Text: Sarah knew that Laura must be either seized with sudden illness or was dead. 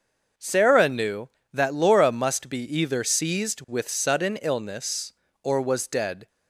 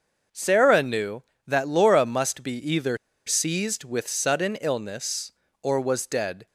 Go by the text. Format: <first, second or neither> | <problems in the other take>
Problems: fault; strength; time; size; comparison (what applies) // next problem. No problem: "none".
first | starts louder than the rest; noticeable; until 1.5 s; 6 dB; noticeable in the first // pauses between "be" and "either"; slight; at 2.5 s; 0.20 s long; slight in the first // pauses between "either" and "seized"; slight; at 2.9 s; 0.29 s long